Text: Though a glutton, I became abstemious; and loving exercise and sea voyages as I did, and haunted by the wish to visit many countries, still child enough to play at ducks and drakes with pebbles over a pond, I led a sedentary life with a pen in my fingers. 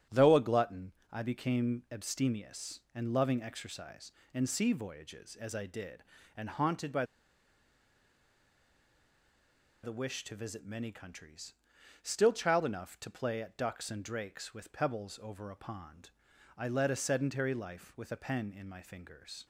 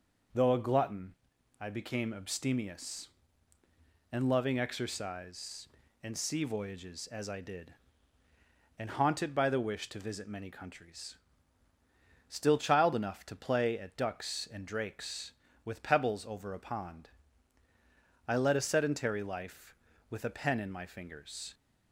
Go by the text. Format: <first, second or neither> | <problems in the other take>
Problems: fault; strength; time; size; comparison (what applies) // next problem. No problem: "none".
second | starts louder than the rest; strong; until 1.3 s; 9 dB // pauses between "by" and "the"; strong; at 7.0 s; 2.7 s long